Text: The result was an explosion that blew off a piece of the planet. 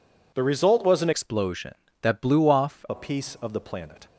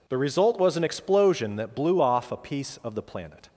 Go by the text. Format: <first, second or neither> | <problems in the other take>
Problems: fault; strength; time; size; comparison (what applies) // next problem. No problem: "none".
second | changes voice from "explosion" to "off"; from 1.1 to 2.8 s; 1.7 s long